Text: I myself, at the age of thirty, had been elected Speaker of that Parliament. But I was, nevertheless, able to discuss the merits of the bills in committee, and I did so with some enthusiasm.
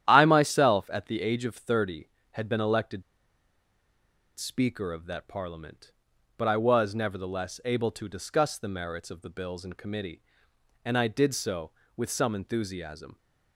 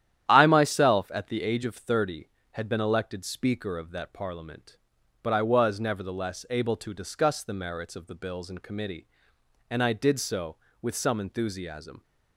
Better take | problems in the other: second | starts louder than the rest; strong; until 1.0 s; 11 dB; strong in the second // pauses between "elected" and "Speaker"; strong; at 3.0 s; 1.3 s long

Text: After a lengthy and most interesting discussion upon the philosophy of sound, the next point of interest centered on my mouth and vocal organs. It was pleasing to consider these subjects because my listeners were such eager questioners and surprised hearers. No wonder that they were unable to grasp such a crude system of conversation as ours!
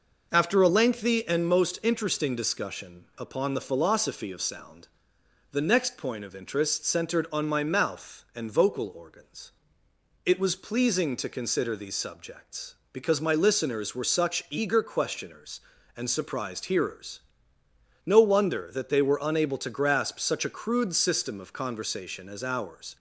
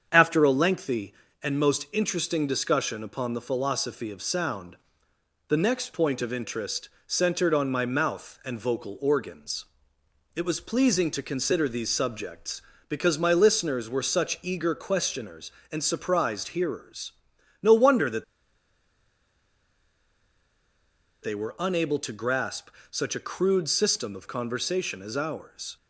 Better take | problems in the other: first | starts louder than the rest; strong; until 1.1 s; 7.5 dB // pauses between "interest" and "centered"; slight; at 6.8 s; 0.18 s long // pauses between "that" and "they"; strong; at 18.2 s; 2.9 s long // pauses between "grasp" and "such"; slight; at 22.7 s; 0.20 s long

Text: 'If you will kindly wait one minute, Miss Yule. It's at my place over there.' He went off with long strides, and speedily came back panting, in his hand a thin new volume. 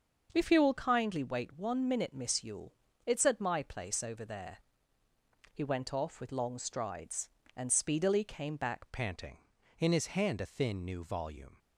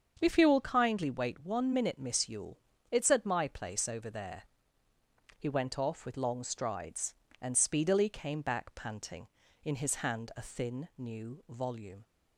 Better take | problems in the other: second | starts louder than the rest; until 1.3 s; 6.5 dB; also in the second // changes voice at "panting"; from 8.9 s on; 2.6 s long

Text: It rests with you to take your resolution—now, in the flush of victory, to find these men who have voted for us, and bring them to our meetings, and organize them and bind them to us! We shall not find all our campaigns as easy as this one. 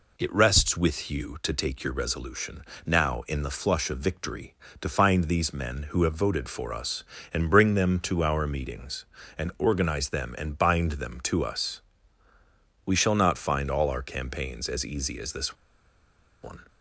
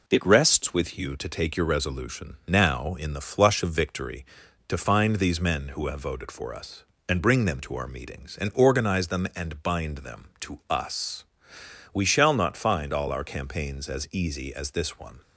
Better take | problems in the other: second | pauses between "this" and "one"; noticeable; at 15.5 s; 0.88 s long

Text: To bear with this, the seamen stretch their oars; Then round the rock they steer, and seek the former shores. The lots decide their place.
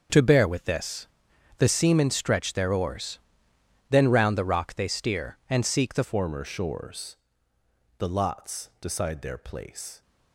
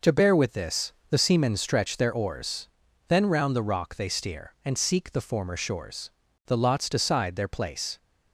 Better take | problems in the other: second | starts louder than the rest; until 1.6 s; 7 dB // changes voice at "former"; from 6.0 s on; 4.0 s long

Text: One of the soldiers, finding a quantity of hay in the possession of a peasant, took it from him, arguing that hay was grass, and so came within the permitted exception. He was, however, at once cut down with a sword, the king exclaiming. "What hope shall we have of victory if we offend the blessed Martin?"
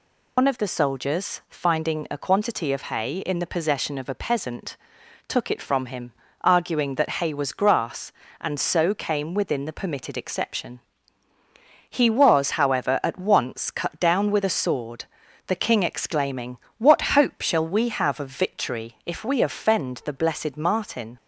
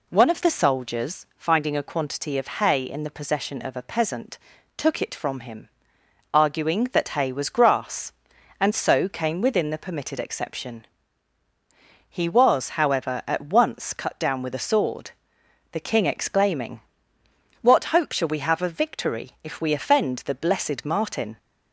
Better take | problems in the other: second | loses the start of "One"; at 0.3 s; 90 ms

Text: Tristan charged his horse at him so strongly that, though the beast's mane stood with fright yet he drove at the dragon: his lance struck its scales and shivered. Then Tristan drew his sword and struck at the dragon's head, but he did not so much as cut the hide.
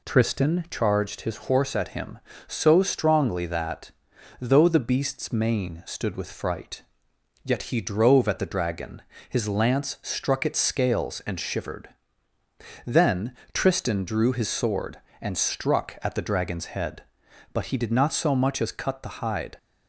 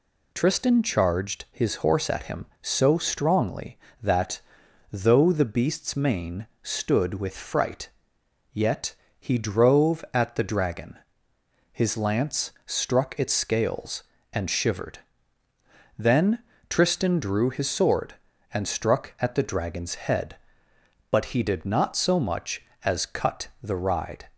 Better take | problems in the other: first | pauses between "mane" and "stood"; slight; at 6.4 s; 0.16 s long // pauses between "fright" and "yet"; noticeable; at 7.8 s; 0.64 s long; noticeable in the first // pauses between "yet" and "he"; slight; at 8.9 s; 0.26 s long // pauses between "Then" and "Tristan"; slight; at 16.3 s; 0.30 s long; slight in the first // says "ride" for "hide"; at 23.7 s

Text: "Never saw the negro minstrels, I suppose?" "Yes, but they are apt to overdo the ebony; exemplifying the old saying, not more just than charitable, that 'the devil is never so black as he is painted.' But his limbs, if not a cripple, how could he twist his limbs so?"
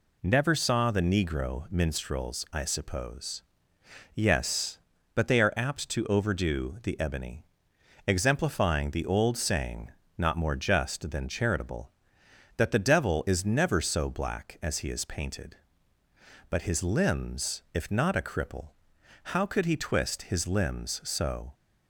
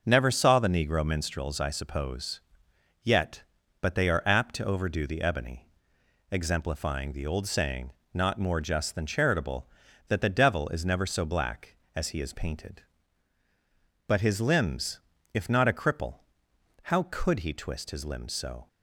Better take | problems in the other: first | starts louder than the rest; until 1.0 s; 6 dB // says "Yet" for "Yes"; at 3.0 s

